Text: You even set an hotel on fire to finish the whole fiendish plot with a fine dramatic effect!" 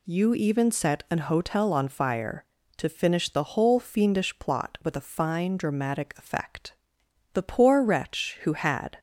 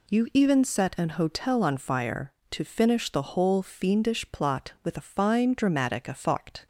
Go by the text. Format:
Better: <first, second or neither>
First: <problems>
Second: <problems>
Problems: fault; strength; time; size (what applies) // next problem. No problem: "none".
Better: second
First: goes on to say "The poor wretch who had"; from 7.3 s on; 1.6 s long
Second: none